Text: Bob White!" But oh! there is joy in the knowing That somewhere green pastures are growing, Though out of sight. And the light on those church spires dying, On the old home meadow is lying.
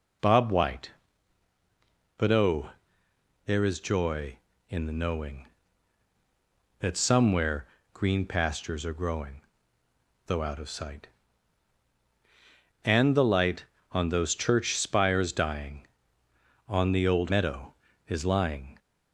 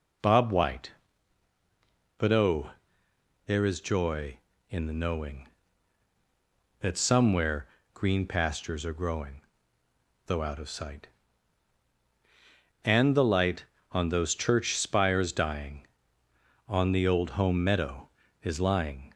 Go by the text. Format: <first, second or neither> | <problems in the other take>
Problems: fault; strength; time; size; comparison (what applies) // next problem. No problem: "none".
second | pauses between "somewhere" and "green"; slight; at 7.6 s; 0.28 s long; slight in the second // skips "home"; at 17.2 s